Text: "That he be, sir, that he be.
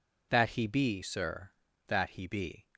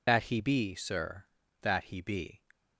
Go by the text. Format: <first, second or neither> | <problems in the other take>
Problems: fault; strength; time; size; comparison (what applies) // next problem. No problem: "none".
first | loses the start of "That"; at 0.0 s; 30 ms